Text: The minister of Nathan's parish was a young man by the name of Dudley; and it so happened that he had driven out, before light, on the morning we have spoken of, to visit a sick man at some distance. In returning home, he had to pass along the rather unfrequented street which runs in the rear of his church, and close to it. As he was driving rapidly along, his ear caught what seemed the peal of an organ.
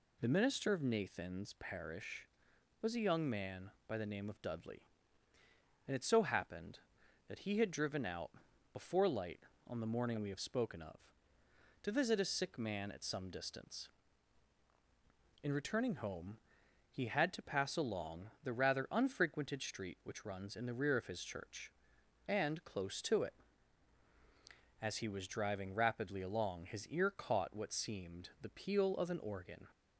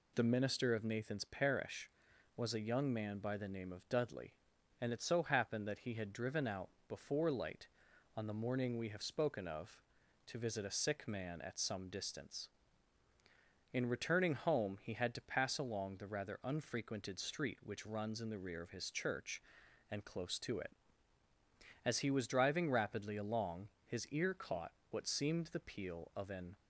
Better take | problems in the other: first | pauses between "caught" and "what"; slight; at 24.7 s; 0.20 s long // stops before "organ"; at 26.5 s

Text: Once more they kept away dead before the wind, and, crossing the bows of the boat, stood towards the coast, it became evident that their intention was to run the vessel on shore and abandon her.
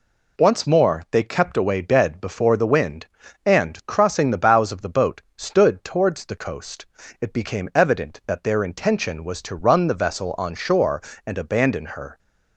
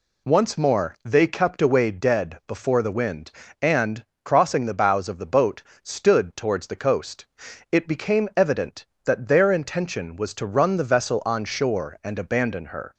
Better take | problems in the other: neither | none

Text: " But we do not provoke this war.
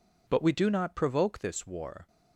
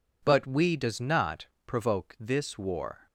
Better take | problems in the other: first | says "does" for "do"; at 0.7 s // pauses between "not" and "provoke"; slight; at 1.4 s; 0.20 s long

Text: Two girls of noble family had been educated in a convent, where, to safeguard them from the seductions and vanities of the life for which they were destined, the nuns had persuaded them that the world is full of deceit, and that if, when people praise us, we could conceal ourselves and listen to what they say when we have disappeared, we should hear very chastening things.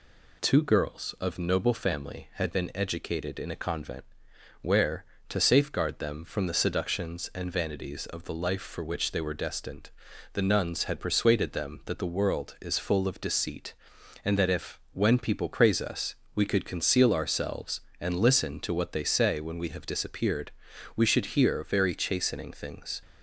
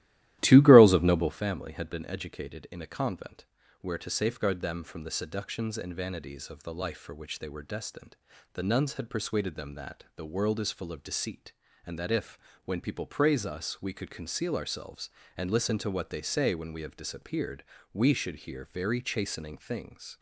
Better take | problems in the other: first | starts louder than the rest; strong; until 1.4 s; 14.5 dB

